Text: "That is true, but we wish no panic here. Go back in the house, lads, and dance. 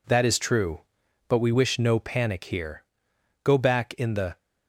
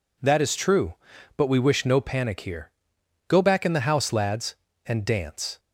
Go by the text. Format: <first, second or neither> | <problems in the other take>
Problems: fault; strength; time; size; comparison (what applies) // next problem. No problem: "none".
second | stops before "house lads and dance"; at 4.4 s